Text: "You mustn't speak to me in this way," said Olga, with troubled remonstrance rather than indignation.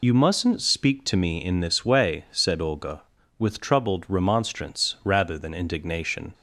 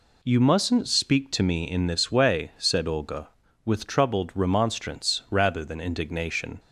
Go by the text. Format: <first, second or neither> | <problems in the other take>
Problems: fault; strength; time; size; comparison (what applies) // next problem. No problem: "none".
second | loses the start of "You"; at 0.0 s; 55 ms